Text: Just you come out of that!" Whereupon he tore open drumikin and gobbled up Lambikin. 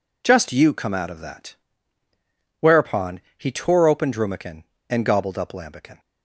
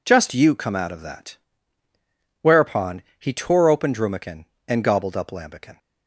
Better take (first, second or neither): neither